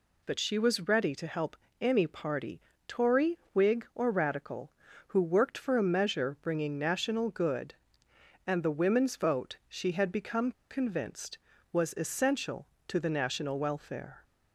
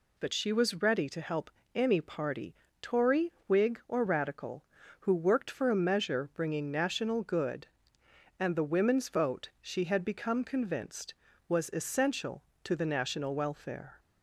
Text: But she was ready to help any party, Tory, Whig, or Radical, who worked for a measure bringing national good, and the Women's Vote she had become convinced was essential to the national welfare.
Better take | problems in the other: second | pauses between "help" and "any"; slight; at 1.5 s; 0.24 s long; slight in the second // pauses between "become" and "convinced"; slight; at 10.5 s; 0.19 s long

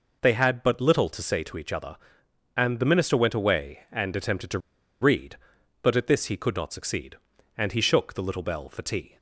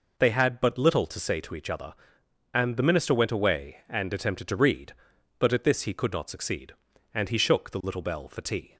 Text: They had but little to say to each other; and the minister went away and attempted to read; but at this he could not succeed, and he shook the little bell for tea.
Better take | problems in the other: second | pauses between "to" and "read"; at 4.5 s; 0.42 s long

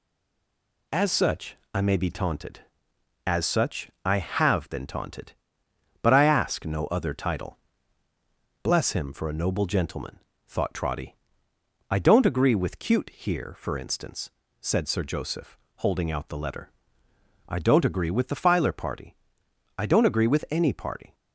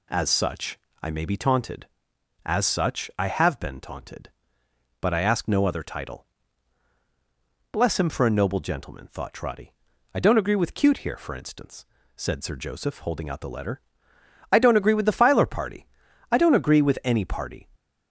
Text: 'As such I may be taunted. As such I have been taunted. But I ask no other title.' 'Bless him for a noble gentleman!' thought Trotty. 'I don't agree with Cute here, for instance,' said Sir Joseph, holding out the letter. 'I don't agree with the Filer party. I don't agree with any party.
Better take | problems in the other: second | stays silent before the first word; slight; until 0.9 s; 0.9 s long // pauses between "such" and "I"; slight; at 1.5 s; 0.18 s long; slight in the second // pauses between "such" and "I"; slight; at 3.9 s; 0.16 s long

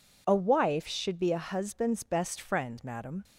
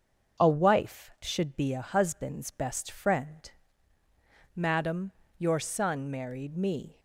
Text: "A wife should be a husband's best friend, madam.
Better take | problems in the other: first | starts louder than the rest; until 1.5 s; 6.5 dB // goes on to say "Your son married me"; from 5.3 s on; 1.6 s long

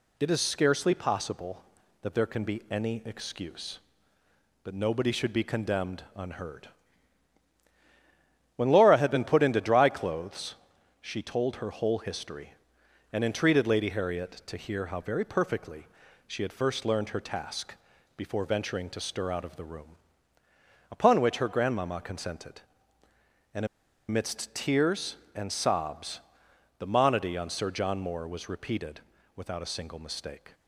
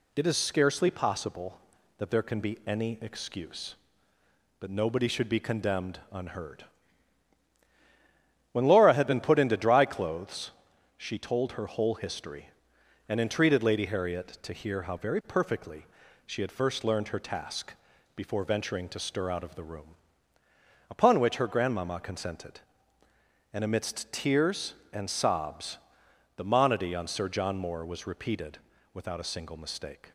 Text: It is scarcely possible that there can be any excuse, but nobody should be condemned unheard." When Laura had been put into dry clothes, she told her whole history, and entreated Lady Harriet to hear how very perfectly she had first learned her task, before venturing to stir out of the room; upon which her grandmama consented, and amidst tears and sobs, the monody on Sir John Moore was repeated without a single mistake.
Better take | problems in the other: second | pauses between "perfectly" and "she"; at 15.8 s; 0.42 s long; also in the second // pauses between "and" and "amidst"; at 23.6 s; 0.41 s long // pauses between "repeated" and "without"; slight; at 28.9 s; 0.36 s long; slight in the second

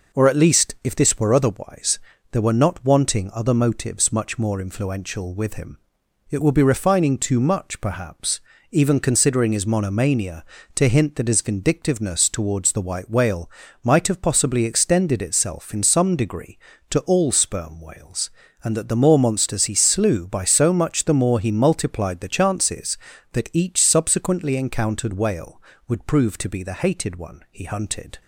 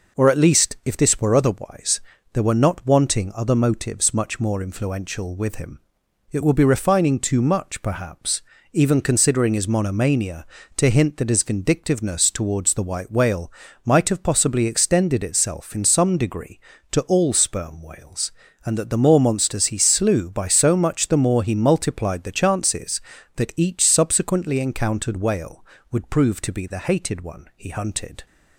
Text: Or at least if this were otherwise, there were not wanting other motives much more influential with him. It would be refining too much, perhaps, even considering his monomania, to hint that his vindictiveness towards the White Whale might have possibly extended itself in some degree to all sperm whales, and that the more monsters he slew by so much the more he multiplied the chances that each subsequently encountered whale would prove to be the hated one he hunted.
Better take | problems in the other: neither | pauses between "Whale" and "might"; slight; the same in both

